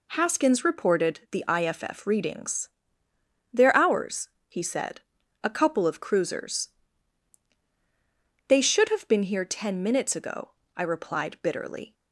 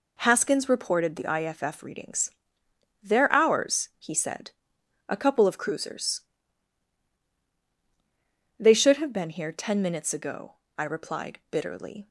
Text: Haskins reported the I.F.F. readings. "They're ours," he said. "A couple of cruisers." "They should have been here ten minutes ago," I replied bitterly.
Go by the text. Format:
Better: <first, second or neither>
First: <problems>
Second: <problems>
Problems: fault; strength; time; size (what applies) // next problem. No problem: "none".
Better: neither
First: none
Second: none